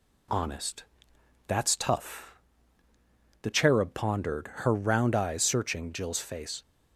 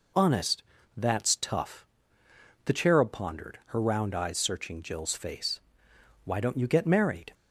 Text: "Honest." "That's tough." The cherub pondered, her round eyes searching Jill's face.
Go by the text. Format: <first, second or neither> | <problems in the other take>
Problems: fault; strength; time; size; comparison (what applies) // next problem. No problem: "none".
first | goes on to say "Why don't you get married"; noticeable; from 6.2 s on; 1.1 s long